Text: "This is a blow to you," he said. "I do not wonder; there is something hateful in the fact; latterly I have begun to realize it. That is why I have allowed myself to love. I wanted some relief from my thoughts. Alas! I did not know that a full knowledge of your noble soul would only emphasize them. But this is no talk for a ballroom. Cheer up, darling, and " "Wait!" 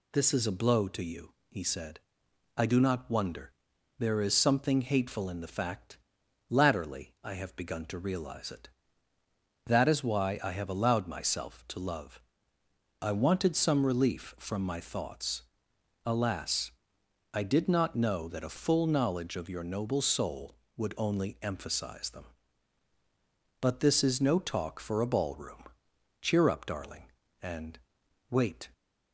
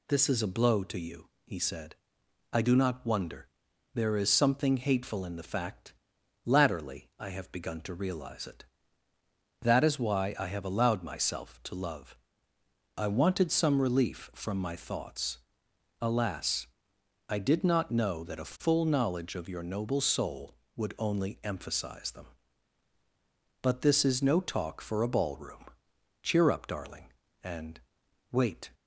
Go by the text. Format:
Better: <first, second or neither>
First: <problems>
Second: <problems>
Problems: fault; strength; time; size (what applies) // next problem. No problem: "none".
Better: neither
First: none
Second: none